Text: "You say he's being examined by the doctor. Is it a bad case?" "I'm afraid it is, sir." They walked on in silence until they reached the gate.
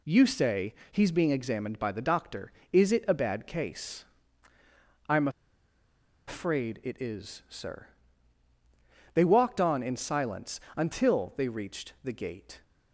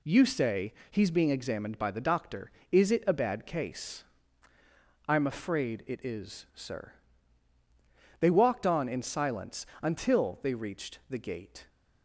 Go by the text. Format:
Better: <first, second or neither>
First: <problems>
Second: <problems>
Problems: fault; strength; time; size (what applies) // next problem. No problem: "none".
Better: second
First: pauses between "say" and "he's"; slight; at 0.7 s; 0.18 s long // pauses between "I'm" and "afraid"; at 5.2 s; 0.98 s long // pauses between "silence" and "until"; slight; at 10.5 s; 0.16 s long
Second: pauses between "say" and "he's"; slight; at 0.7 s; 0.18 s long // pauses between "silence" and "until"; slight; at 9.6 s; 0.16 s long